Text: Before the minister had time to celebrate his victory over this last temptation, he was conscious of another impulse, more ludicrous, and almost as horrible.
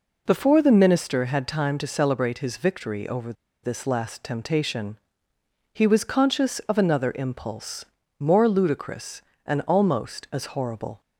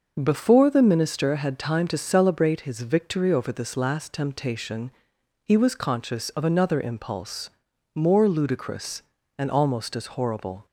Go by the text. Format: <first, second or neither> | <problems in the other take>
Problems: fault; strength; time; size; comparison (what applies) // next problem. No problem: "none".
second | pauses between "over" and "this"; slight; at 3.3 s; 0.30 s long